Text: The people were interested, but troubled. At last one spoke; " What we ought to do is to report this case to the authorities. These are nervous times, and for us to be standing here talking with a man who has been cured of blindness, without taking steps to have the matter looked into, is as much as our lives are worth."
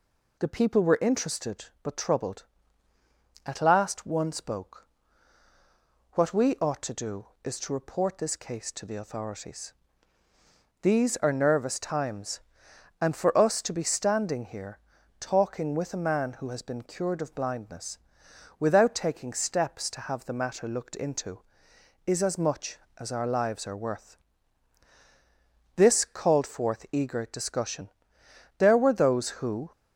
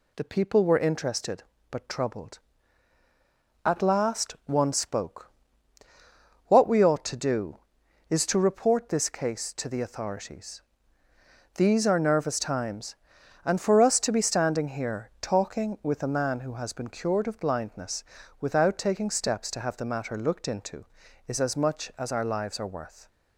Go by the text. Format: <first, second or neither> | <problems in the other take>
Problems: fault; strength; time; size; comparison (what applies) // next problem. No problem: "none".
second | pauses between "here" and "talking"; at 14.7 s; 0.42 s long // goes on to say "This called forth eager discussion there were those who"; strong; from 25.7 s on; 3.9 s long